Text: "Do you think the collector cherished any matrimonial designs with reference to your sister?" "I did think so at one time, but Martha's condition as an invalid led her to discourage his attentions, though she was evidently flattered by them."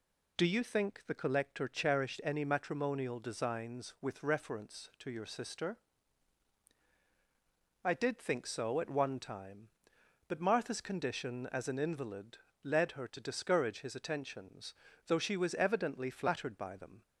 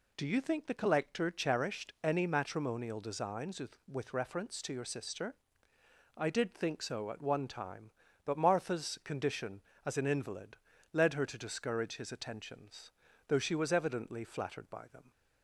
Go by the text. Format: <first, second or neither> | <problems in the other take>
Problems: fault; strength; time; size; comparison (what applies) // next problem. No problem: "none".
first | says "with" twice; at 3.8 s // pauses between "invalid" and "led"; slight; at 10.5 s; 0.36 s long; slight in the first